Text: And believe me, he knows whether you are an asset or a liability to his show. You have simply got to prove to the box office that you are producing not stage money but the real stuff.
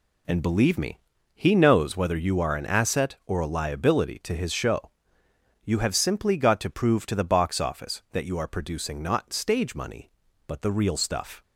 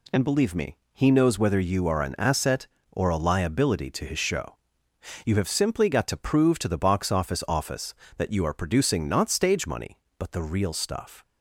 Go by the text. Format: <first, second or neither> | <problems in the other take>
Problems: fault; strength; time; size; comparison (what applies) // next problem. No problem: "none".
first | says "office" twice; at 7.4 s